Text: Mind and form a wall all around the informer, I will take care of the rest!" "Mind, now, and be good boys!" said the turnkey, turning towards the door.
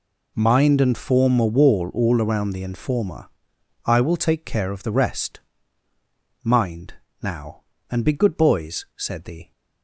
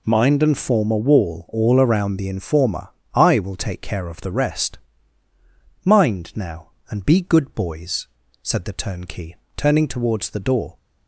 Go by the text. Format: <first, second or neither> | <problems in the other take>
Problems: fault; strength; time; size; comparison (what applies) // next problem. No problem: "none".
second | stops before "turnkey turning towards the door"; at 9.5 s